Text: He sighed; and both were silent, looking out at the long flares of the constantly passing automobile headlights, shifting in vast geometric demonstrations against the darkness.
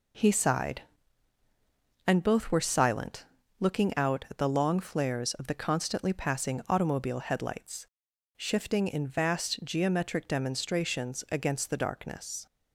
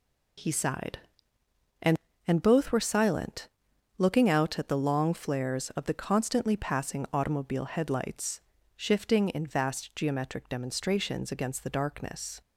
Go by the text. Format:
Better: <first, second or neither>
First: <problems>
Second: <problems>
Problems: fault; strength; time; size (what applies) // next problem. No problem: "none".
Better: first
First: none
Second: says "and" twice; at 2.2 s